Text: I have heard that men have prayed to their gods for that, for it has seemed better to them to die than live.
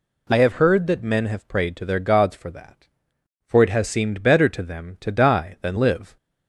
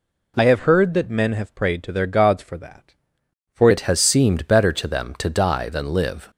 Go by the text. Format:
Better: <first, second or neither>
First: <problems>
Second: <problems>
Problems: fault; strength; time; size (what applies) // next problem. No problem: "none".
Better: first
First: none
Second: changes voice at "it"; from 3.7 s on; 2.6 s long